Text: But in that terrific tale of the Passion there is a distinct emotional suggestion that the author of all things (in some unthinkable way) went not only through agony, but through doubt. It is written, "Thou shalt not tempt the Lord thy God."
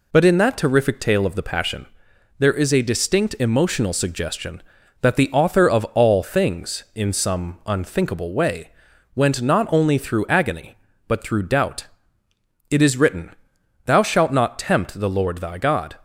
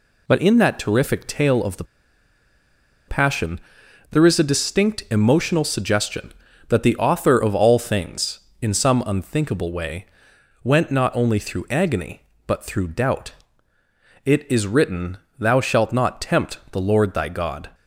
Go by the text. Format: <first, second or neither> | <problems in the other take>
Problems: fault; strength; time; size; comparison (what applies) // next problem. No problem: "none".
first | pauses between "the" and "Passion"; at 1.8 s; 1.2 s long // pauses between "Passion" and "there"; noticeable; at 3.5 s; 0.52 s long; noticeable in the first